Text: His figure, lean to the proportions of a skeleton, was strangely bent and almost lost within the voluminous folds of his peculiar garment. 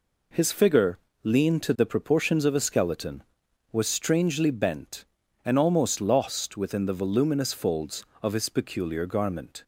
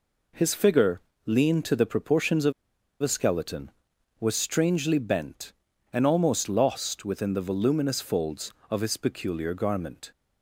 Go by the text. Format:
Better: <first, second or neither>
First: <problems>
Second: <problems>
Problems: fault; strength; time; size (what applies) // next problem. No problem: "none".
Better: first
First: none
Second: pauses between "of" and "a"; noticeable; at 2.5 s; 0.50 s long